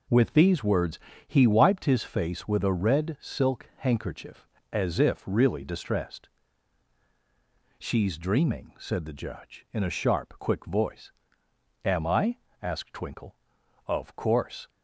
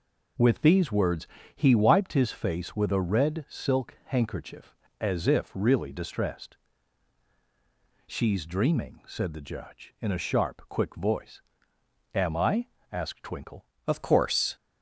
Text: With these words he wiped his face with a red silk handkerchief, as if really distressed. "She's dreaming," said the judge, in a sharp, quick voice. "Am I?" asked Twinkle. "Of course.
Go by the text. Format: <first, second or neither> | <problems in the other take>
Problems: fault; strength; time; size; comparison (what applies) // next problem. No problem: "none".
first | pauses between "words" and "he"; slight; at 1.2 s; 0.28 s long; slight in the first // changes voice at "Of"; from 13.8 s on; 0.7 s long